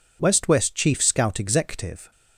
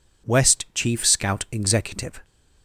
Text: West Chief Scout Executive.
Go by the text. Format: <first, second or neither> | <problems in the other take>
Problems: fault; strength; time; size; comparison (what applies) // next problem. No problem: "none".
second | says "West" twice; at 0.4 s